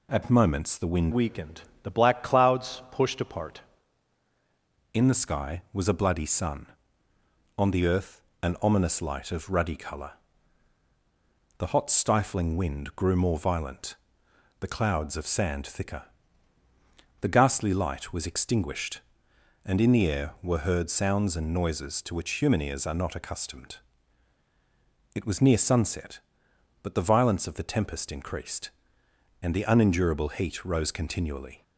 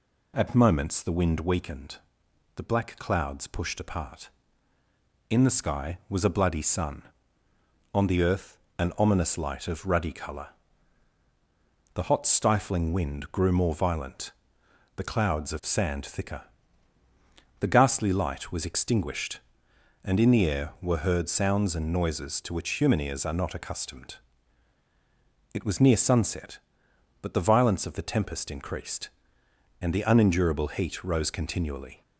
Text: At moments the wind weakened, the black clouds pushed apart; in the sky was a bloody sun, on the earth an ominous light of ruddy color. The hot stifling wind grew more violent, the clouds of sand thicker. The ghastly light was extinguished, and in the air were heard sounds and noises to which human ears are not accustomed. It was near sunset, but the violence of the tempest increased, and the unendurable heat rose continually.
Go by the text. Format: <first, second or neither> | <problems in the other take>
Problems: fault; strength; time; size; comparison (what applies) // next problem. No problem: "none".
second | changes voice from "weakened" to "apart"; from 1.1 to 3.6 s; 2.5 s long // pauses between "earth" and "an"; slight; at 8.2 s; 0.20 s long; slight in the second